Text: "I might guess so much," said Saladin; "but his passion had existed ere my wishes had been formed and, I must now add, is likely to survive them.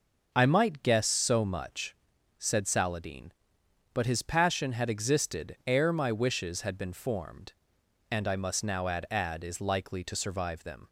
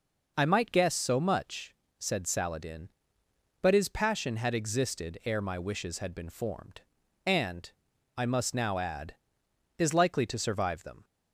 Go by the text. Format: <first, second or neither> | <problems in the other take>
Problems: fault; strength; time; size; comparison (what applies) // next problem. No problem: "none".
second | says "add" twice; at 9.1 s